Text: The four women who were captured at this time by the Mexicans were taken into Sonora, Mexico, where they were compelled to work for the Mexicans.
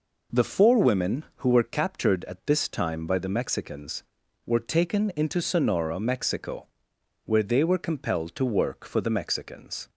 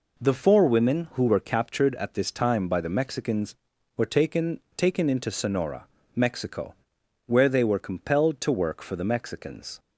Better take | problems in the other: first | says "taken" twice; at 4.7 s

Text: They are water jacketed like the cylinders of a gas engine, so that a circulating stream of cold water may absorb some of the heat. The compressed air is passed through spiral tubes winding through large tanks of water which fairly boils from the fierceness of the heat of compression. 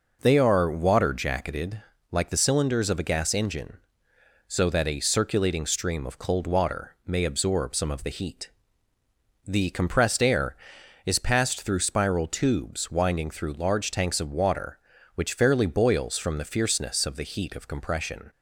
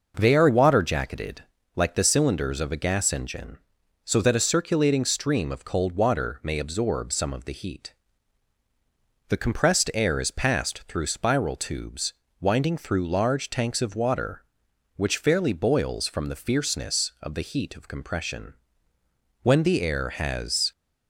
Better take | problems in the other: first | pauses between "jacketed" and "like"; slight; at 1.4 s; 0.36 s long; slight in the first // pauses between "tubes" and "winding"; slight; at 12.1 s; 0.26 s long // goes on to say "When the air has"; noticeable; from 19.4 s on; 1.3 s long

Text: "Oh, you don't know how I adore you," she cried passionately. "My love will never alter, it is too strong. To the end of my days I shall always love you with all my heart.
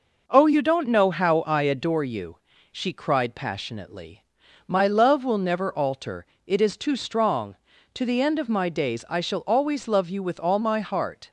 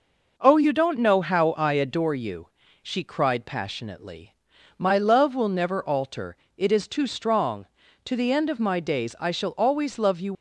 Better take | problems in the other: first | stops before "with all my heart"; at 10.3 s

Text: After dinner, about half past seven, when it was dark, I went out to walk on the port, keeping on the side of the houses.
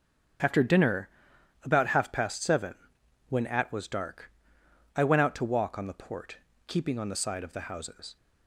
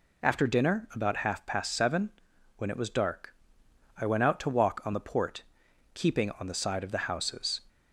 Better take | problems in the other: second | starts louder than the rest; strong; until 1.9 s; 8 dB // says "at" for "it"; at 3.4 s

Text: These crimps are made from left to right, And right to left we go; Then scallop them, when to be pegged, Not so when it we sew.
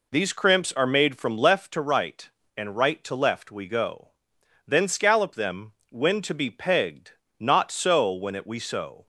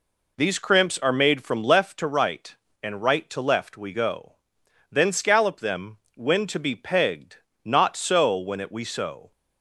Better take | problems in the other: neither | none

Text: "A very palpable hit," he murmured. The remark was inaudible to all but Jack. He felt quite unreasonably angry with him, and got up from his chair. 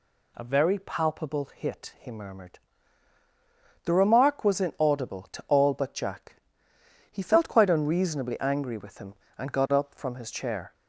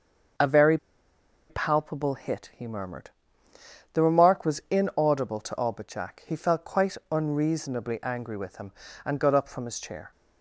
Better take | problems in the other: first | starts louder than the rest; until 2.1 s; 6.5 dB // pauses between "very" and "palpable"; noticeable; at 0.7 s; 0.73 s long

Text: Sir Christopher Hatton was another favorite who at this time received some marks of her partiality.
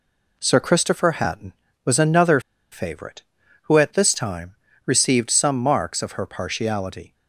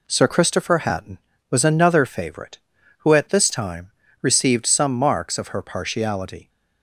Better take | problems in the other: second | pauses between "another" and "favorite"; slight; at 2.3 s; 0.32 s long // pauses between "time" and "received"; slight; at 4.5 s; 0.30 s long; slight in the second

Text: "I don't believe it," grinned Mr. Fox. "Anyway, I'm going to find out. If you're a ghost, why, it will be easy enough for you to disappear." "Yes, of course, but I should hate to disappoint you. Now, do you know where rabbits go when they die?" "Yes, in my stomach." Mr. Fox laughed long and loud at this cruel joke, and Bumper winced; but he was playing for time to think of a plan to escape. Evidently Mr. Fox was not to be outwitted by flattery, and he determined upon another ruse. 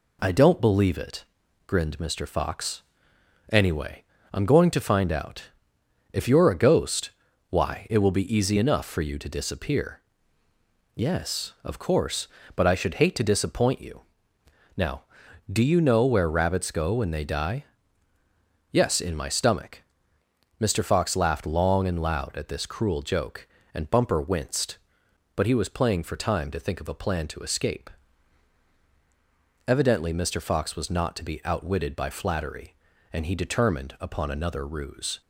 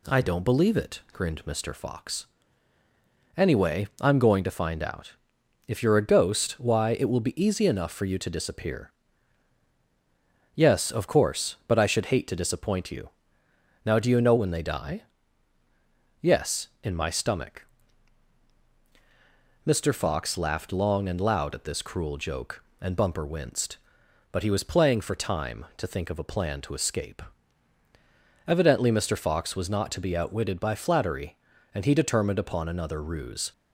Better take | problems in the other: first | skips "where rabbits go"; at 14.3 s

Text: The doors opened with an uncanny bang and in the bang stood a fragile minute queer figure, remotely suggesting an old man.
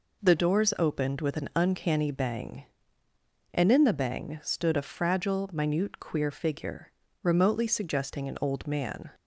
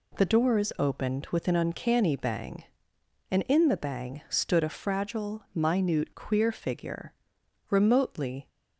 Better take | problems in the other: first | stops before "suggesting an old man"; at 8.4 s

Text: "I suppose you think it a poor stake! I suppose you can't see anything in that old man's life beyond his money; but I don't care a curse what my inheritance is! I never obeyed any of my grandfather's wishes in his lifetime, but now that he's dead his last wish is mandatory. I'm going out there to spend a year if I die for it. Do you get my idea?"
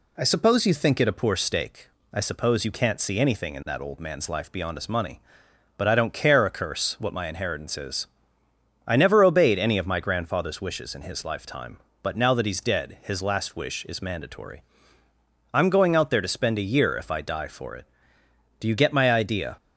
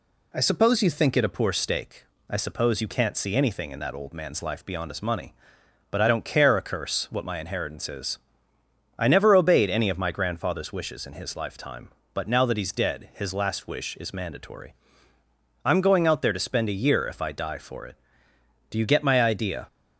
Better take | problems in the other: neither | none

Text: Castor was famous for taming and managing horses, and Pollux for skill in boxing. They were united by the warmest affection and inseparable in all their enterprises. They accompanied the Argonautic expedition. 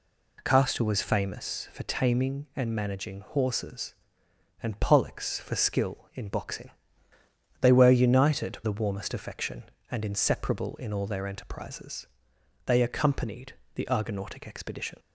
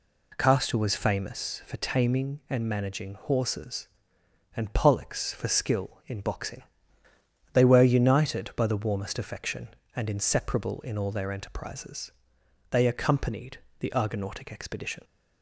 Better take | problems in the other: second | skips "by"; at 8.6 s // pauses between "accompanied" and "the"; slight; at 13.5 s; 0.22 s long; slight in the second

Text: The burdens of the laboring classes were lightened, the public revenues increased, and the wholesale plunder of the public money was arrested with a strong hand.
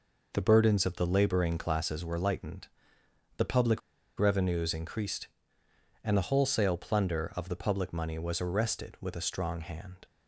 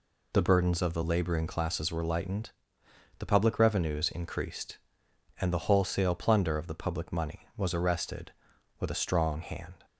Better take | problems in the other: second | pauses between "public" and "revenues"; at 3.8 s; 0.38 s long

